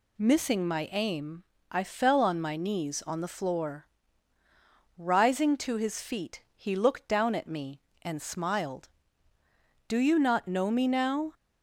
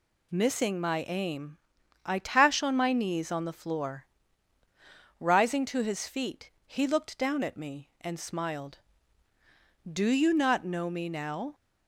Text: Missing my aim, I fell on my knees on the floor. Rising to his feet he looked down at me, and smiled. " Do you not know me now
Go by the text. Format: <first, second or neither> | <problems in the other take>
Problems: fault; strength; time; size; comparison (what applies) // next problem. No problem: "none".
first | says "tash" for "fell"; at 2.1 s // pauses between "feet" and "he"; slight; at 6.5 s; 0.16 s long